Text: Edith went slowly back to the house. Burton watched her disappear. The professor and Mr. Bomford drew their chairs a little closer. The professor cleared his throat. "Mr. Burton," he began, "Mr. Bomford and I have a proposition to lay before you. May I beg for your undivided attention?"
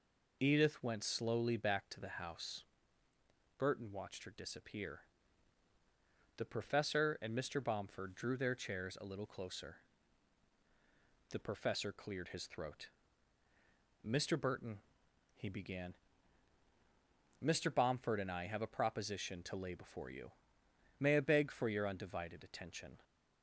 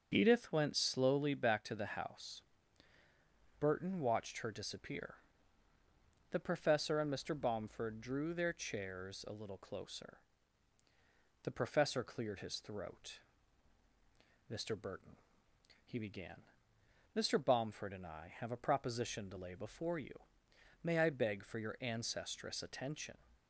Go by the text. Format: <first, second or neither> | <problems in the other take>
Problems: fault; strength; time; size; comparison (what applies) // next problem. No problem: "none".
first | starts louder than the rest; until 1.1 s; 6.5 dB // says "ancestress" for "undivided"; at 21.8 s